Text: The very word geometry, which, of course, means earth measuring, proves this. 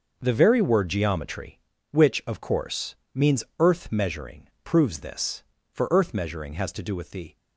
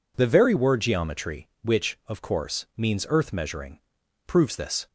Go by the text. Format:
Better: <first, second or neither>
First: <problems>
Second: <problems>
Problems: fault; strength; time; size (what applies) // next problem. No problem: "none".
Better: second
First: starts louder than the rest; noticeable; until 1.2 s; 6 dB // pauses between "means" and "earth"; slight; at 3.4 s; 0.16 s long // goes on to say "For earth measuring has to do with the"; from 5.7 s on; 1.6 s long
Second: none